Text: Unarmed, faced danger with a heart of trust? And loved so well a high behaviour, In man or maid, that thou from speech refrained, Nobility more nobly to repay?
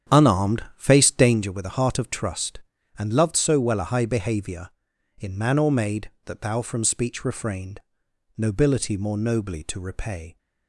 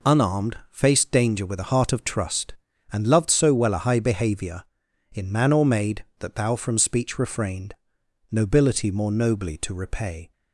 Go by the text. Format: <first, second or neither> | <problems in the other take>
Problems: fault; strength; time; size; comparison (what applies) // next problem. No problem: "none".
second | starts louder than the rest; strong; until 1.5 s; 9 dB